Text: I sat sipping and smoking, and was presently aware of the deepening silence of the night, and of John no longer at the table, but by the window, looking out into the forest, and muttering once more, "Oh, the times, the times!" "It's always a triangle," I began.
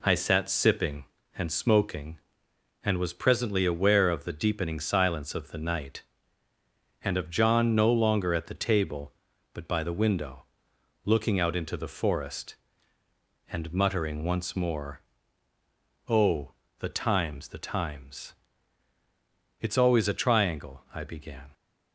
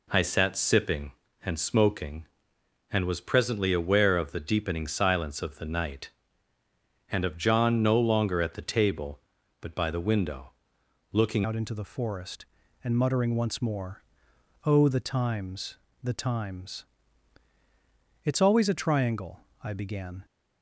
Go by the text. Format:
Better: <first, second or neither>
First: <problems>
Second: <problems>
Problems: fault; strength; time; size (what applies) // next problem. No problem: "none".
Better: first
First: none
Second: changes voice at "out"; from 11.4 s on; 8.8 s long